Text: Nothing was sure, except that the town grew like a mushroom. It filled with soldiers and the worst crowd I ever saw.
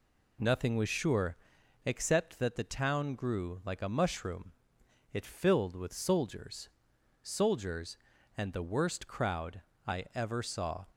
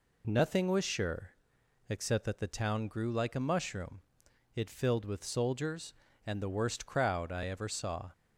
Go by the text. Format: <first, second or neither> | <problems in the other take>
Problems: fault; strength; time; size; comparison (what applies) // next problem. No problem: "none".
second | says "soldiers" twice; at 7.2 s // pauses between "crowd" and "I"; slight; at 9.5 s; 0.26 s long